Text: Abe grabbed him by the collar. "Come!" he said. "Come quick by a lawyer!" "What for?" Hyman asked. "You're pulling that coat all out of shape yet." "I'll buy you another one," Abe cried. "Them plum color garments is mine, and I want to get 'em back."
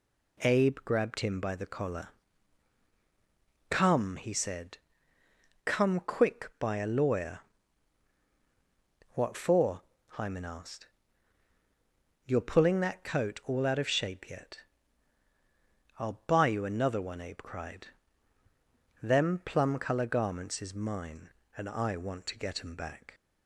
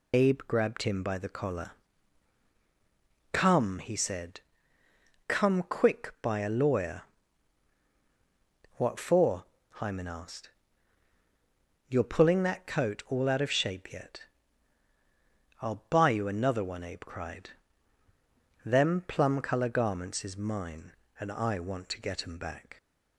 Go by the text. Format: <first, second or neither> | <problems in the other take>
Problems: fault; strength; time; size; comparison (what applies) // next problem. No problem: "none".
first | loses the start of "Abe"; at 0.1 s; 115 ms